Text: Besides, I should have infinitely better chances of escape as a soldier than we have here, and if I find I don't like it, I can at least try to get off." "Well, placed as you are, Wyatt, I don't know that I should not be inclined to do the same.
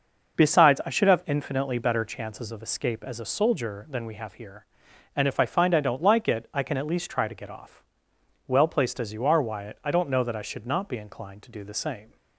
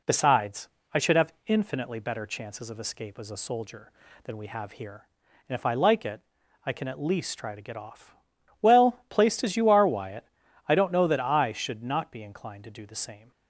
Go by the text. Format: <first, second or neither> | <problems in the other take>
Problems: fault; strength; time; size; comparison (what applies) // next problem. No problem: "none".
first | skips "find I don't"; at 5.7 s